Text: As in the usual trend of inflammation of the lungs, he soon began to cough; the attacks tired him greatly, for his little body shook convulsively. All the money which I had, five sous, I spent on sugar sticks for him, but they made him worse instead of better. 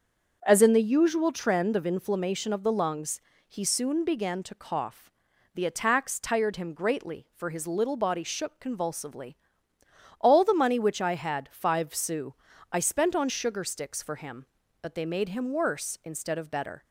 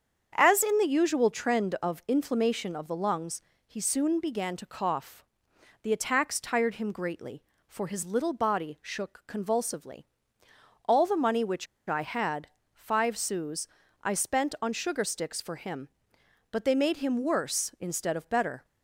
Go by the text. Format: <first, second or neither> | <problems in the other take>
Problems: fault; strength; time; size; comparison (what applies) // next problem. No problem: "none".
first | starts louder than the rest; strong; until 1.3 s; 7.5 dB; also in the first // pauses between "which" and "I"; slight; at 11.6 s; 0.22 s long